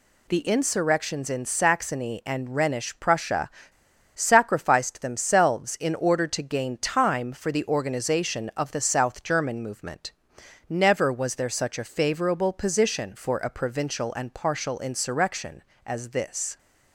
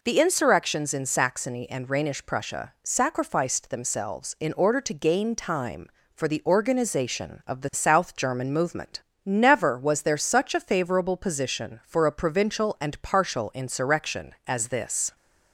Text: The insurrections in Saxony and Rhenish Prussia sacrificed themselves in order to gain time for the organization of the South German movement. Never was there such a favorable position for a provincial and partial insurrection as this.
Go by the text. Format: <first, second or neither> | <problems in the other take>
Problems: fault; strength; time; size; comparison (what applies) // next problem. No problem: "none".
second | pauses between "Prussia" and "sacrificed"; noticeable; at 3.4 s; 0.65 s long